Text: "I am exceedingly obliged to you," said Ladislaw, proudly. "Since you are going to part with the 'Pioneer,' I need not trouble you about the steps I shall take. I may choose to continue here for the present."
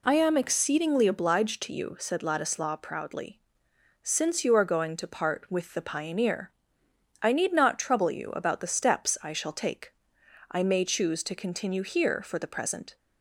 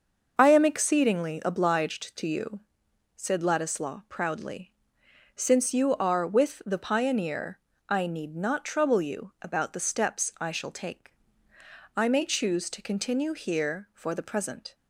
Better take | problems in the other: first | starts louder than the rest; noticeable; until 1.3 s; 6 dB // skips "going to part"; at 6.2 s

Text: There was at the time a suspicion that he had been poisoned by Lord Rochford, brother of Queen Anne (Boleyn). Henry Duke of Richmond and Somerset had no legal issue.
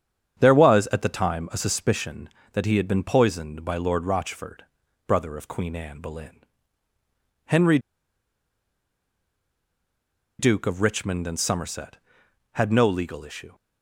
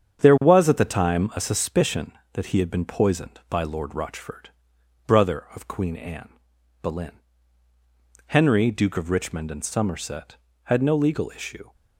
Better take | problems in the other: second | starts louder than the rest; strong; until 1.4 s; 8 dB; strong in the second // pauses between "Henry" and "Duke"; strong; at 7.7 s; 2.6 s long

